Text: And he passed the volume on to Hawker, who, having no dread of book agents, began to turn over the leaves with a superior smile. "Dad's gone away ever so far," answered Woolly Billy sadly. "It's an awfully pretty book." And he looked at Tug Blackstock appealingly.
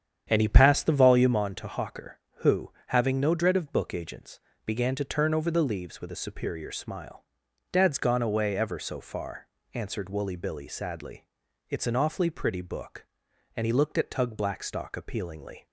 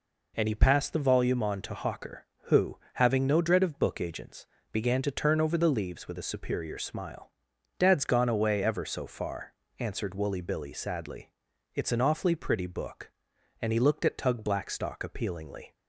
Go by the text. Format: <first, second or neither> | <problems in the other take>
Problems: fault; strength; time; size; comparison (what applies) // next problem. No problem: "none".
second | starts louder than the rest; strong; until 1.5 s; 8.5 dB